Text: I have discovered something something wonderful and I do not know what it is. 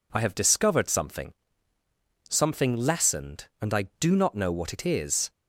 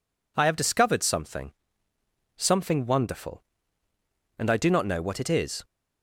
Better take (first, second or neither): second